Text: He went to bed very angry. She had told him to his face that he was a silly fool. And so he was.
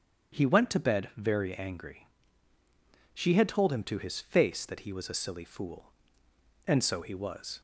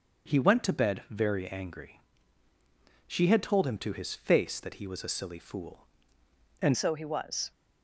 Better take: first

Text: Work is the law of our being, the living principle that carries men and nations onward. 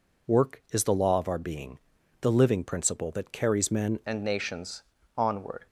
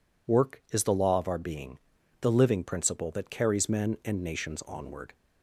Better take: second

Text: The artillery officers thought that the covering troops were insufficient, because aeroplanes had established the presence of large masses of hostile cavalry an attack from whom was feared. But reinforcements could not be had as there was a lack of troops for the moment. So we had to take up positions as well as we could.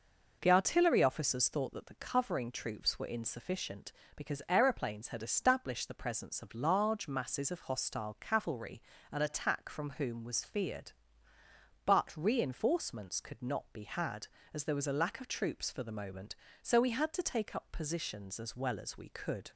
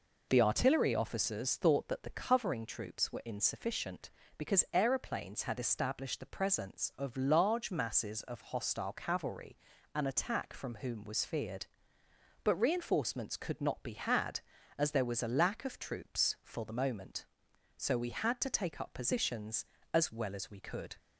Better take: neither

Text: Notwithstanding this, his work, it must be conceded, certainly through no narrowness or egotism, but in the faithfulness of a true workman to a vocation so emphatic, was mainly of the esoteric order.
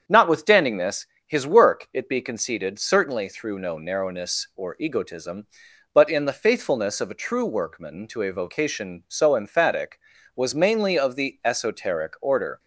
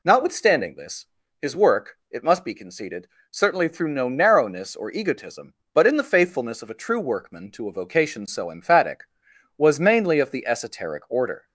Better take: second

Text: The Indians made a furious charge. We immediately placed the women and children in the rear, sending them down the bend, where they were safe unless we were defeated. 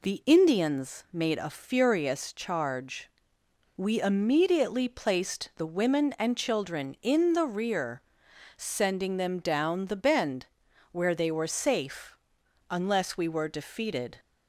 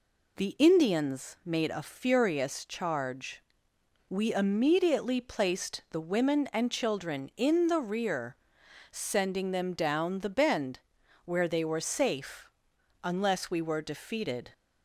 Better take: neither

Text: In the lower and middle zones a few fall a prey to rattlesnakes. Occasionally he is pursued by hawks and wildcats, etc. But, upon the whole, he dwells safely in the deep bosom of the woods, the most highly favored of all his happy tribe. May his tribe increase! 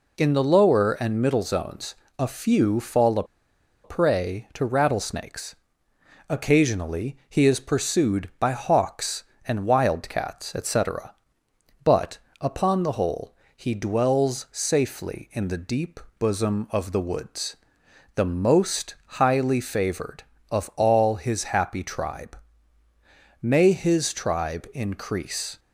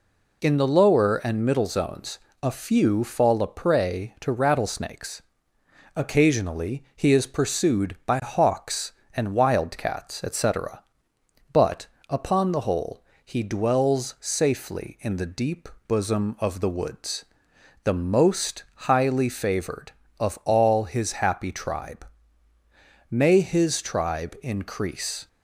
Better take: second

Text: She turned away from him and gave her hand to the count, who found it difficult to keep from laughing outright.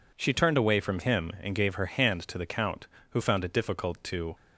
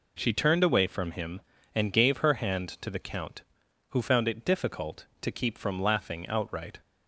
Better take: second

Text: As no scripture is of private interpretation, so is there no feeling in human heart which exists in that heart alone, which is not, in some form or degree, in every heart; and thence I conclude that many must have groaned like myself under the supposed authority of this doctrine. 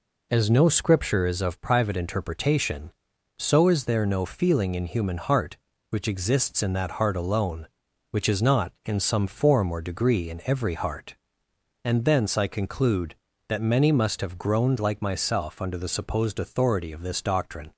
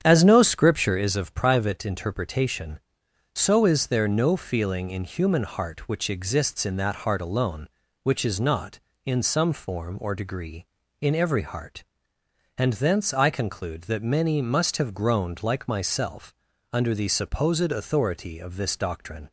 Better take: first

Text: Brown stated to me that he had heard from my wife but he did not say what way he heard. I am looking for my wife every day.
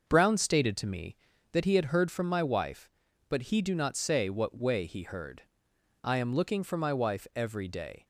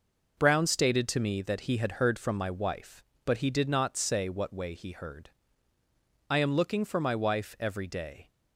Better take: second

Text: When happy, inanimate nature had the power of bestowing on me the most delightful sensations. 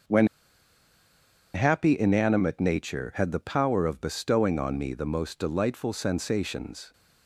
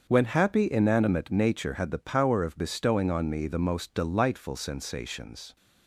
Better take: second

